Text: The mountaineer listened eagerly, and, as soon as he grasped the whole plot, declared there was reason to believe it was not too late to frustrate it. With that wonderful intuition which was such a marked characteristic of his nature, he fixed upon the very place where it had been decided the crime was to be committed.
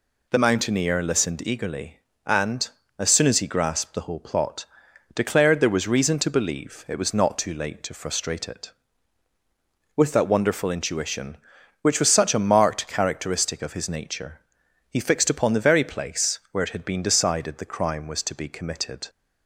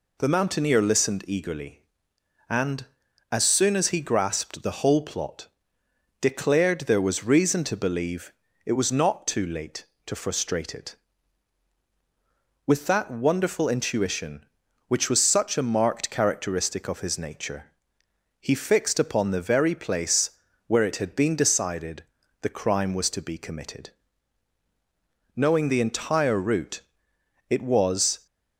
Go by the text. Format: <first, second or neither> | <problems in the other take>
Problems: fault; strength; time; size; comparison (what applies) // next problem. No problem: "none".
first | pauses between "believe" and "it"; slight; at 8.3 s; 0.34 s long // pauses between "place" and "where"; slight; at 20.3 s; 0.36 s long // pauses between "decided" and "the"; at 22.0 s; 0.38 s long // goes on to say "Knowing the entire route it was"; strong; from 25.3 s on; 2.9 s long